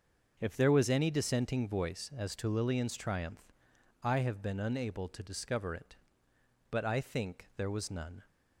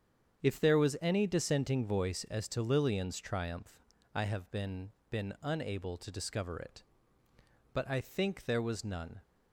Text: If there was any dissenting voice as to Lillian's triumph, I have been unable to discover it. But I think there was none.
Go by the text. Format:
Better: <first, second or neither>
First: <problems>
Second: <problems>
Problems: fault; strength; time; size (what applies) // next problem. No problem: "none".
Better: first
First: starts louder than the rest; until 1.4 s; 6 dB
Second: starts louder than the rest; strong; until 1.4 s; 8 dB // says "been" twice; at 5.0 s